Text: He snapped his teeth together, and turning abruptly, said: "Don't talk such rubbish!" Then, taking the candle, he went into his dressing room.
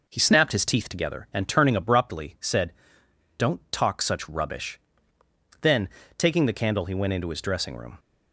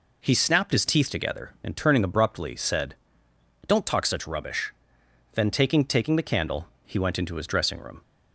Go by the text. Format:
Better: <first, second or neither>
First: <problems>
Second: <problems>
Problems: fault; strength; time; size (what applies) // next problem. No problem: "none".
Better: first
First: none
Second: says "taking" twice; at 5.8 s